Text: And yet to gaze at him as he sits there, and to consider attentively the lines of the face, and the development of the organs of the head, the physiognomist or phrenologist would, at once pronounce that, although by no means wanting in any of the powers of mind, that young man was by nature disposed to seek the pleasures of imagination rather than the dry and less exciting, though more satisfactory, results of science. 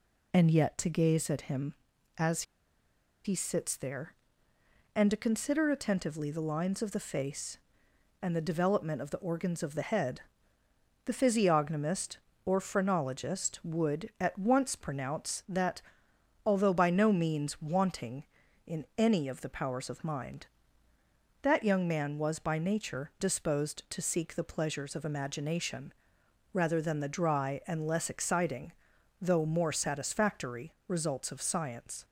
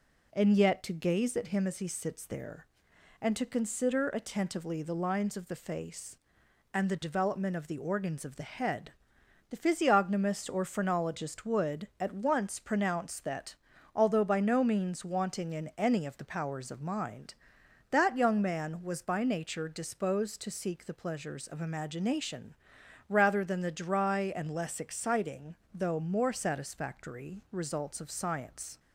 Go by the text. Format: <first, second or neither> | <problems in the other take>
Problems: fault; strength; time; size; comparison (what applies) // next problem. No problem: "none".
second | pauses between "as" and "he"; noticeable; at 2.4 s; 0.81 s long // pauses between "imagination" and "rather"; noticeable; at 25.9 s; 0.60 s long; noticeable in the second